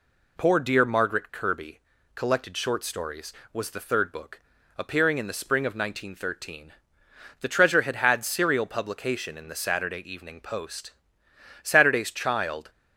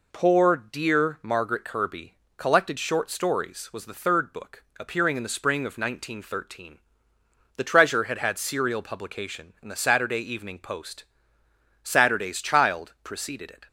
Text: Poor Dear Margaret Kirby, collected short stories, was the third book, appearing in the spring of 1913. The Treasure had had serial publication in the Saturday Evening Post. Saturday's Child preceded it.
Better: second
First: stops before "preceded it"; at 12.7 s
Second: none

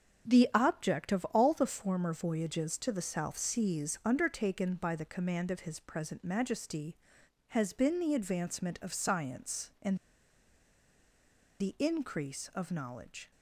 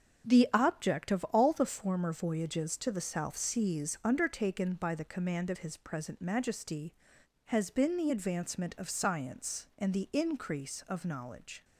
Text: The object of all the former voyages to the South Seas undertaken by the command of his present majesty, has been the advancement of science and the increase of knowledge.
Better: second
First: starts louder than the rest; until 1.3 s; 7 dB // pauses between "and" and "the"; strong; at 9.9 s; 1.6 s long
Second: starts louder than the rest; until 1.3 s; 7 dB

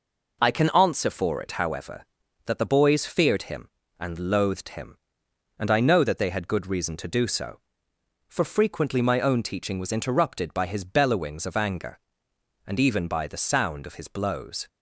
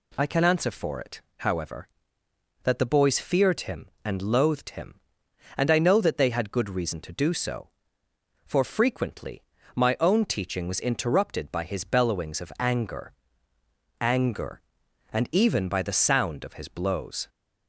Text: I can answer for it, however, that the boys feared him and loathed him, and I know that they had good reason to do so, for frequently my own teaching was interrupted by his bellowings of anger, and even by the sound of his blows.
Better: first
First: none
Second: pauses between "frequently" and "my"; slight; at 9.4 s; 0.32 s long // says "anger" twice; at 14.0 s

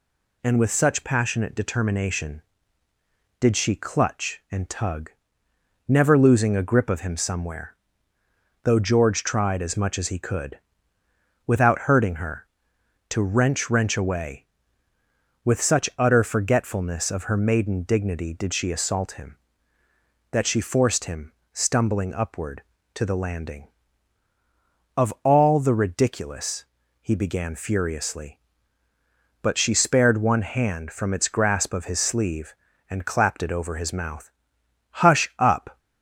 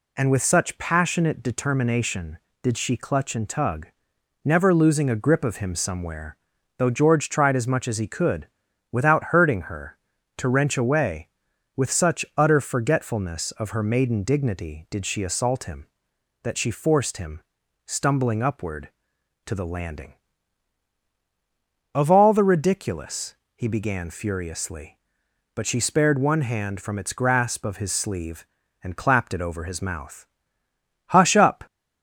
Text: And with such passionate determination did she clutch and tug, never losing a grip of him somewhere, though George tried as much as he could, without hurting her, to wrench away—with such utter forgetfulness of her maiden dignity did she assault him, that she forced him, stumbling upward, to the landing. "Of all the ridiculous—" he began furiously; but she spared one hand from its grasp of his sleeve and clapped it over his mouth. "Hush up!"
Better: second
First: says "wrench" twice; at 13.6 s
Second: none

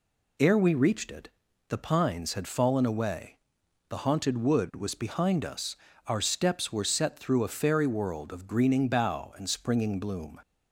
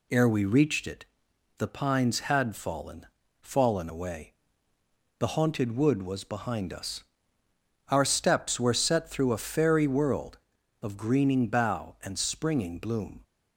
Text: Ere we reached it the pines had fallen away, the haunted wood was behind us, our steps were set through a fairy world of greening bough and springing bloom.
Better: first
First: pauses between "it" and "the"; at 1.2 s; 0.40 s long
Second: pauses between "it" and "the"; noticeable; at 1.0 s; 0.52 s long // says "fallen" twice; at 3.4 s

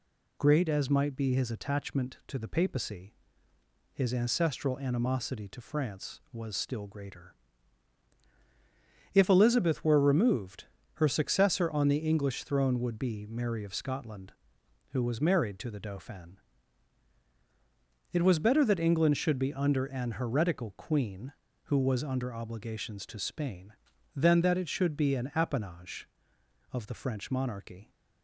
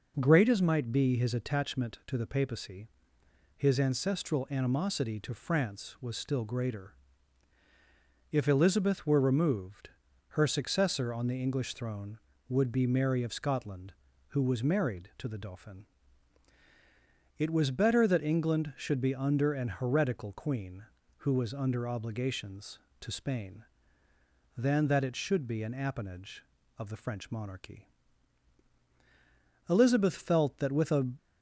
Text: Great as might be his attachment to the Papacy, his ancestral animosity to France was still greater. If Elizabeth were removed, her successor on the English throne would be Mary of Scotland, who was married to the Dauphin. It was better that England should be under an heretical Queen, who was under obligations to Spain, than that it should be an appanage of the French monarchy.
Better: first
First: none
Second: goes on to say "Elizabeth felt that with a"; from 29.6 s on; 1.4 s long

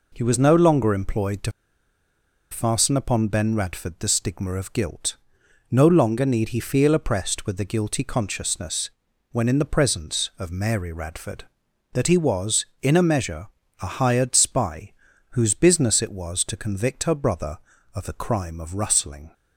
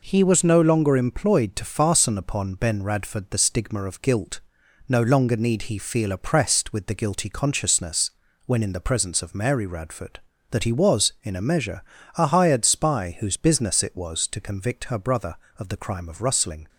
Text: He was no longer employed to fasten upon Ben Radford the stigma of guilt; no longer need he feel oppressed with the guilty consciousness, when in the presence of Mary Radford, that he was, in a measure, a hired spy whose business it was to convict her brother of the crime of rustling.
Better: second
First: pauses between "to" and "fasten"; at 1.5 s; 0.99 s long // pauses between "spy" and "whose"; at 14.9 s; 0.38 s long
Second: none

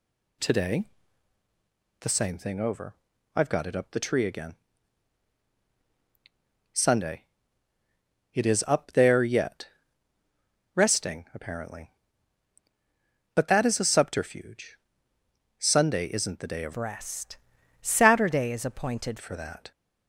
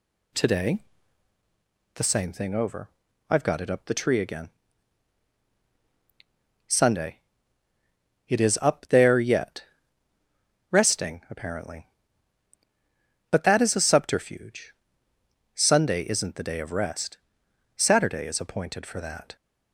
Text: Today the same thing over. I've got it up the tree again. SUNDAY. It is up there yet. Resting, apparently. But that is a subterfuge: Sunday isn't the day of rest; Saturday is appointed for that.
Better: second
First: pauses between "Today" and "the"; at 0.8 s; 1.1 s long // changes voice from "rest" to "appointed"; from 16.7 to 19.1 s; 2.4 s long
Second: pauses between "Today" and "the"; at 0.8 s; 1.1 s long

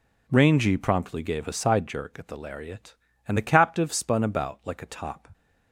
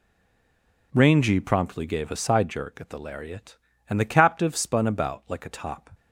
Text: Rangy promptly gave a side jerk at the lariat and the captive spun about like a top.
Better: first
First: none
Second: stays silent before the first word; slight; until 0.9 s; 0.9 s long

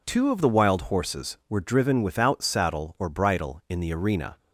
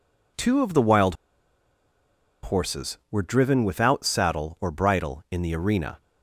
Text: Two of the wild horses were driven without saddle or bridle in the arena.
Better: first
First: none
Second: pauses between "wild" and "horses"; strong; at 1.1 s; 1.2 s long

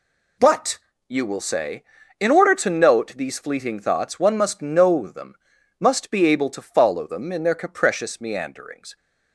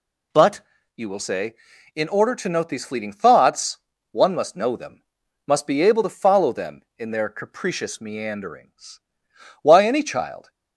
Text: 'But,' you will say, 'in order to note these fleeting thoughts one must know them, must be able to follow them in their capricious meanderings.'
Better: first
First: none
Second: pauses between "thoughts" and "one"; slight; at 3.7 s; 0.34 s long // goes on to say "Why any child"; noticeable; from 9.6 s on; 0.86 s long

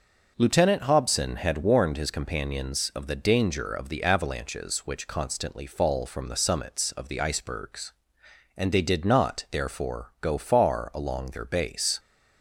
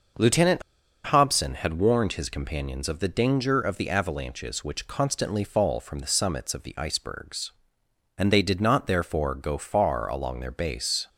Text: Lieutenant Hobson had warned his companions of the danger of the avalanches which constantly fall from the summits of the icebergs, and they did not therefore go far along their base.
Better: first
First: none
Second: pauses between "Lieutenant" and "Hobson"; at 0.6 s; 0.44 s long

